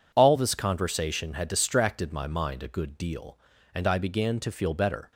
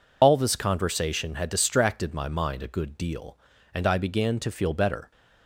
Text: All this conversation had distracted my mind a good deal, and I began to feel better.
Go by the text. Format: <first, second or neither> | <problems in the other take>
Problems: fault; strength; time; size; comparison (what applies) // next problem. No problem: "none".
first | loses the start of "All"; at 0.2 s; 75 ms